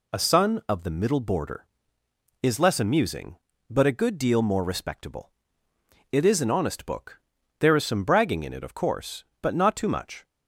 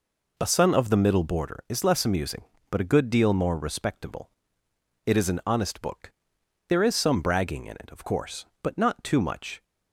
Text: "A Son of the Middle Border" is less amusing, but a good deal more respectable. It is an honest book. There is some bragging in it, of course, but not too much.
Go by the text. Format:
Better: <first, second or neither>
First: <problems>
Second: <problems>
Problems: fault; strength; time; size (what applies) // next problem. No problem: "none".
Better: first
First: none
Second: starts louder than the rest; noticeable; until 1.4 s; 4 dB